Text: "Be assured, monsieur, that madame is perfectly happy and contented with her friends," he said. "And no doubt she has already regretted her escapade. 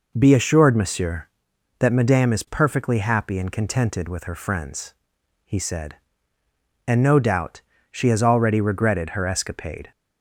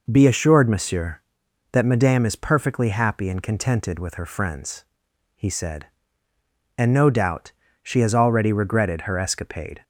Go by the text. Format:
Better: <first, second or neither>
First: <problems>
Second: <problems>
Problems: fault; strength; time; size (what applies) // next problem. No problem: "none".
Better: neither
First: pauses between "doubt" and "she"; slight; at 7.6 s; 0.30 s long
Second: pauses between "doubt" and "she"; slight; at 7.5 s; 0.31 s long